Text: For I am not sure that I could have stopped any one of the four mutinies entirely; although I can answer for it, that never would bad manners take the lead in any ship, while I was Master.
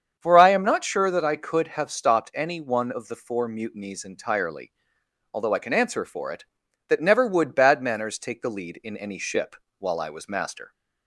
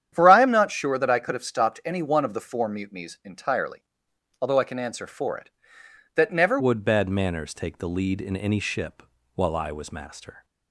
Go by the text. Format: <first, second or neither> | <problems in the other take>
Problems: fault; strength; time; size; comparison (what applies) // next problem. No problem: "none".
first | starts louder than the rest; strong; until 1.1 s; 9.5 dB; strong in the first // changes voice at "would"; from 6.5 s on; 3.9 s long